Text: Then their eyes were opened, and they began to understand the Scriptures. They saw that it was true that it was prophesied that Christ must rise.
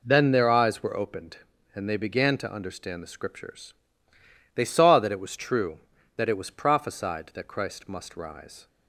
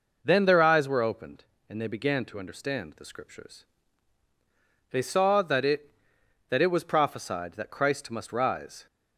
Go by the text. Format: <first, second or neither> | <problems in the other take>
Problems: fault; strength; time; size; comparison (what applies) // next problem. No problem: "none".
first | skips "was true"; at 6.1 s